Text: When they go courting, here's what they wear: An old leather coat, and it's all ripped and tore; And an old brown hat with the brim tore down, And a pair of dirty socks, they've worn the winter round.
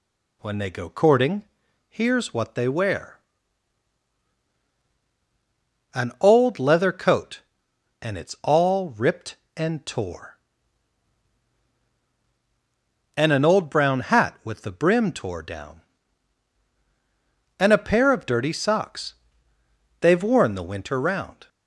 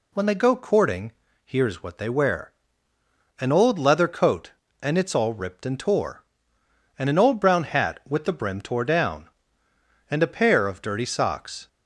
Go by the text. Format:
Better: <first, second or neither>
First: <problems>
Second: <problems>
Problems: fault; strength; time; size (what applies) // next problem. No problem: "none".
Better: first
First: none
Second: stops before "they've worn the winter round"; at 11.6 s